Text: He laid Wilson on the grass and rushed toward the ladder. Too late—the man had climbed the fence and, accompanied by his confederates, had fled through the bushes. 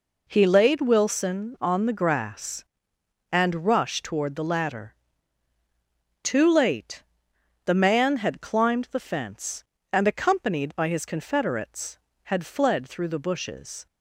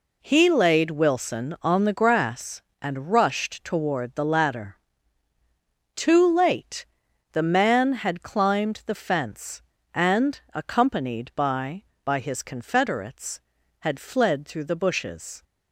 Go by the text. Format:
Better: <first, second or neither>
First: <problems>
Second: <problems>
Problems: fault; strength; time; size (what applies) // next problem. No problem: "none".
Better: first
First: none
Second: says "by" twice; at 12.0 s